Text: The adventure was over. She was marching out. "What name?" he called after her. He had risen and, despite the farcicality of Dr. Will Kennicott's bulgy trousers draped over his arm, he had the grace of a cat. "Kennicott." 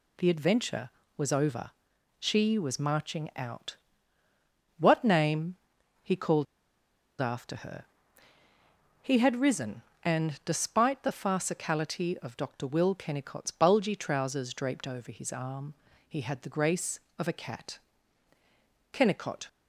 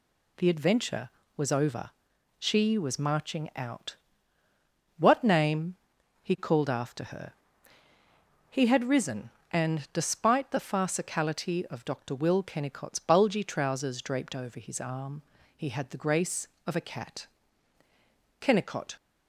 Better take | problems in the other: second | pauses between "called" and "after"; noticeable; at 6.4 s; 0.76 s long

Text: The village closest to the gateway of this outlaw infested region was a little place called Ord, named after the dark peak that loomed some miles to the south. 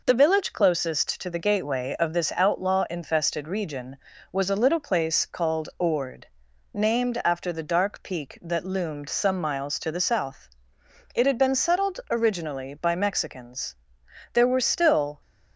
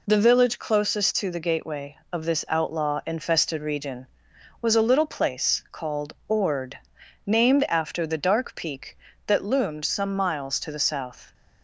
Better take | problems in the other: second | goes on to say "It had been settled originally by Mexicans there were still"; strong; from 11.1 s on; 4.0 s long

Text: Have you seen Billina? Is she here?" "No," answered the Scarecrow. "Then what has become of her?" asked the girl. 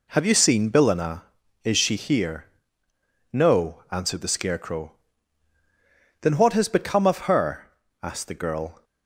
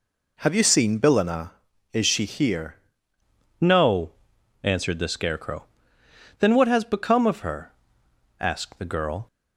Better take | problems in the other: first | changes voice at "No"; from 3.5 s on; 5.7 s long

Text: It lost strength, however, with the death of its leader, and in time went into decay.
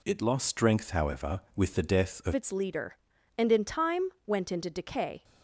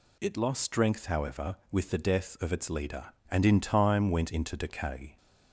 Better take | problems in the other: second | changes voice at "its"; from 2.3 s on; 2.9 s long // pauses between "time" and "went"; slight; at 4.0 s; 0.16 s long

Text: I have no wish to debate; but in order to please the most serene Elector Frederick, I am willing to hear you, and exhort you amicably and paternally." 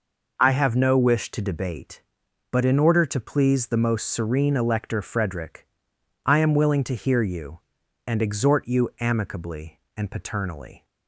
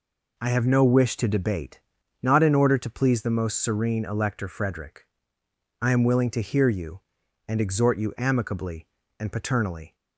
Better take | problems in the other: first | says "not" for "but"; at 2.2 s

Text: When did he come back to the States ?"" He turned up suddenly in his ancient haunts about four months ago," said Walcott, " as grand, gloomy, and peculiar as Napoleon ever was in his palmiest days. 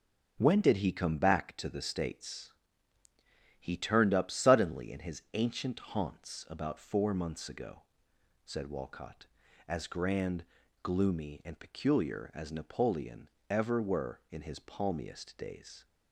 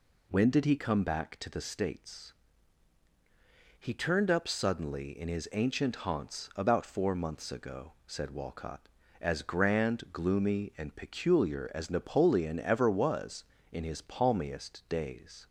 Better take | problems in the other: second | pauses between "Napoleon" and "ever"; slight; at 13.2 s; 0.22 s long // says "were" for "was"; at 13.8 s

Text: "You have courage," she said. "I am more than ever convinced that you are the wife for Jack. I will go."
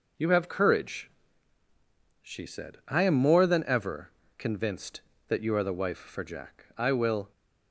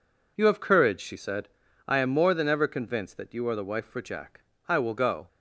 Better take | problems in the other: second | pauses between "ever" and "convinced"; slight; at 4.1 s; 0.26 s long // stops before "go"; at 7.3 s

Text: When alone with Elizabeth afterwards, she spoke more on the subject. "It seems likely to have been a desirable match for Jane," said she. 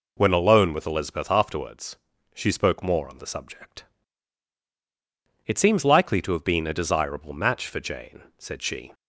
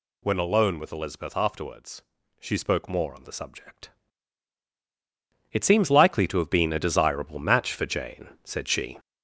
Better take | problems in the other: first | gets louder; noticeable; throughout; 4 dB

